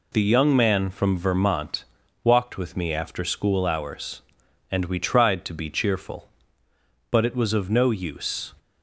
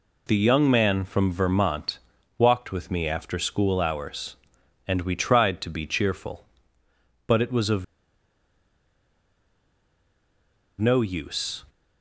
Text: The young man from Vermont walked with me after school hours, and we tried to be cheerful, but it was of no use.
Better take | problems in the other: first | pauses between "Vermont" and "walked"; at 1.9 s; 0.38 s long; also in the first // pauses between "of" and "no"; strong; at 7.8 s; 2.9 s long

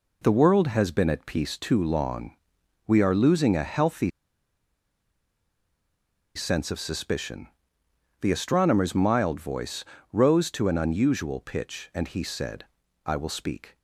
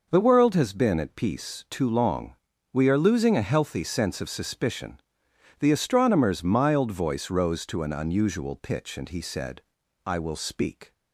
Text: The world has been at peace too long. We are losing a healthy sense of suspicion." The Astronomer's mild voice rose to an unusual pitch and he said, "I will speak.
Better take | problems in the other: second | pauses between "healthy" and "sense"; strong; at 4.0 s; 2.2 s long // pauses between "voice" and "rose"; slight; at 9.8 s; 0.30 s long

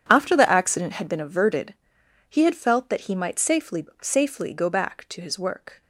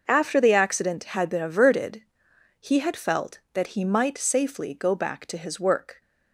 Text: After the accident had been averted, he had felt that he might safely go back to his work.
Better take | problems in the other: second | says "safely" twice; at 4.0 s

